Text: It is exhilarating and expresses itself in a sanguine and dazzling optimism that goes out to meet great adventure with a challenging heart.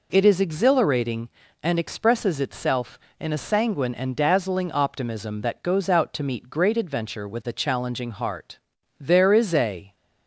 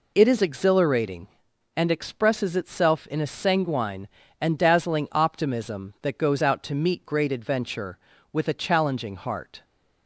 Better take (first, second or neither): second